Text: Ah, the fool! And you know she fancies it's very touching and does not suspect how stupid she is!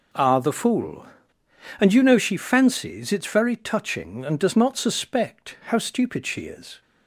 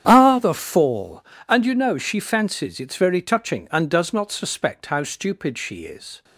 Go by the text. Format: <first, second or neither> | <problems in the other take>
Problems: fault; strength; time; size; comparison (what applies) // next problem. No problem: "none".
first | starts louder than the rest; strong; until 1.0 s; 9.5 dB // says "fall" for "fool"; at 0.5 s